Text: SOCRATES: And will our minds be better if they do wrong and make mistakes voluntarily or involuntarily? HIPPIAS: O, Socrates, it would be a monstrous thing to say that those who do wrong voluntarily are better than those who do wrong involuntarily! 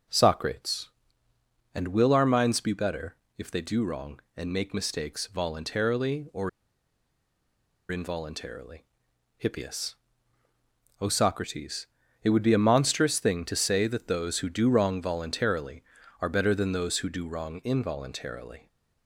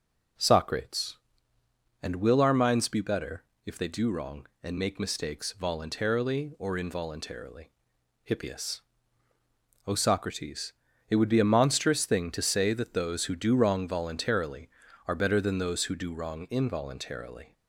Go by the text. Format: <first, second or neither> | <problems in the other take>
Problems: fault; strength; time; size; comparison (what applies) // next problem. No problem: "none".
second | pauses between "better" and "if"; slight; at 3.1 s; 0.20 s long; slight in the second // pauses between "or" and "involuntarily"; strong; at 6.4 s; 1.3 s long